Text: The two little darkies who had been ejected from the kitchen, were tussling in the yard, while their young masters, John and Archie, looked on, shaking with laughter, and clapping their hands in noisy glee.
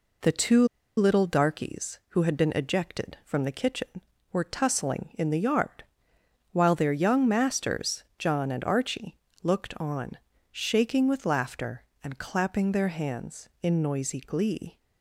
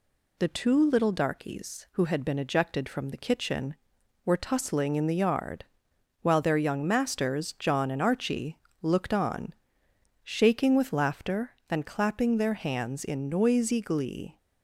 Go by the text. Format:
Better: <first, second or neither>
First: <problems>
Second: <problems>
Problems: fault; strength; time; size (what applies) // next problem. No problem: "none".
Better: second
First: pauses between "two" and "little"; slight; at 0.6 s; 0.30 s long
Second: none